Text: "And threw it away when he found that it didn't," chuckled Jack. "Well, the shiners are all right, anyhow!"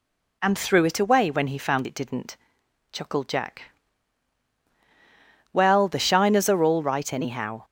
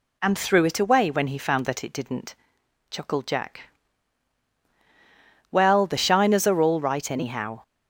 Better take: second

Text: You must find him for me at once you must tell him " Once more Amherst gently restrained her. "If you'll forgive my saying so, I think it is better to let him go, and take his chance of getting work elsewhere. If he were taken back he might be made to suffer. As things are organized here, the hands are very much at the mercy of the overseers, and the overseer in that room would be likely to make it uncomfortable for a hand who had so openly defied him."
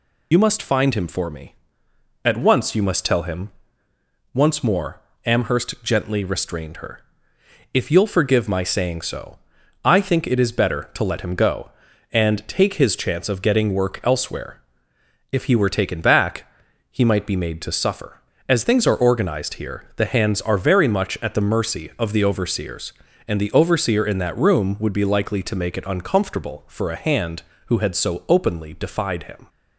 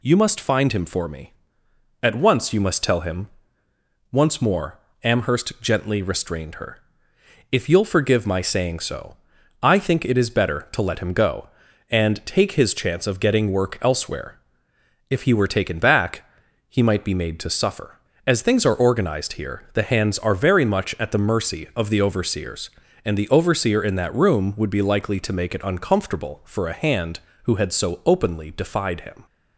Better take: second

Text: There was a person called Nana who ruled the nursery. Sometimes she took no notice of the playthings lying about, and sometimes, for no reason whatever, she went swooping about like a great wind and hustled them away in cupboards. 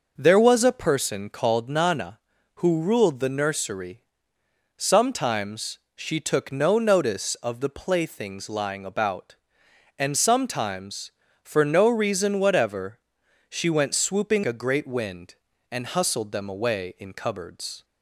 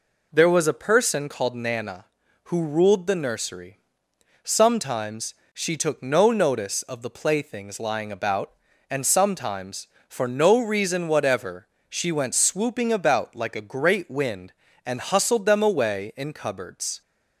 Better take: second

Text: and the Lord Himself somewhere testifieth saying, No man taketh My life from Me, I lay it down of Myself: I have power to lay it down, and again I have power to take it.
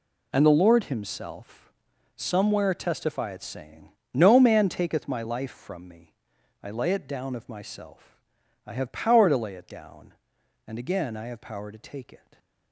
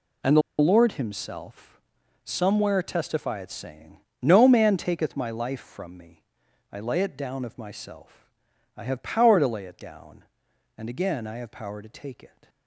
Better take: first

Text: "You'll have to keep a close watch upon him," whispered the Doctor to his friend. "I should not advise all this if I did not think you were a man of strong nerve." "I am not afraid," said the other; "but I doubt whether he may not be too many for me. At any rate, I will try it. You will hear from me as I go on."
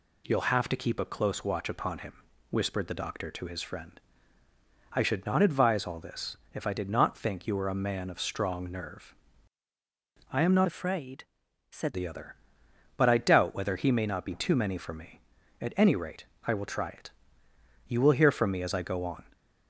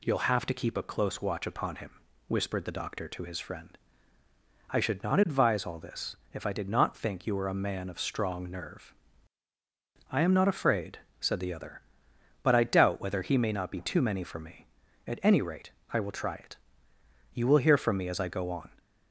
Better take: second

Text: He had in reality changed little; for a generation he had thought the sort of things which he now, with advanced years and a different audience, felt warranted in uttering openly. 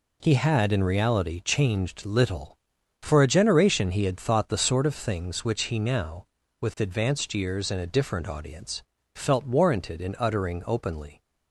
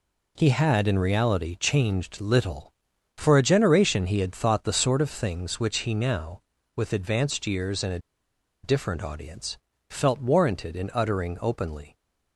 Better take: first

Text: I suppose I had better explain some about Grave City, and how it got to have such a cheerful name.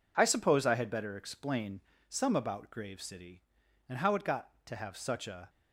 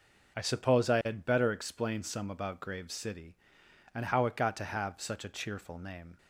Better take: second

